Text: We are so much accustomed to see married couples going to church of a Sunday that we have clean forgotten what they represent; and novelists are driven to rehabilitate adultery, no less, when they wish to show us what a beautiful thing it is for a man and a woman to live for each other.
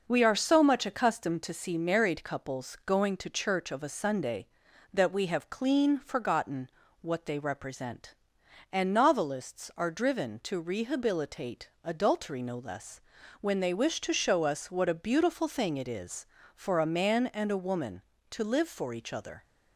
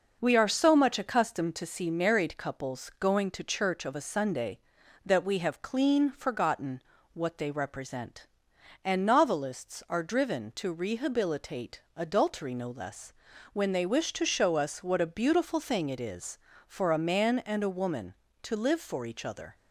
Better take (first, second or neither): neither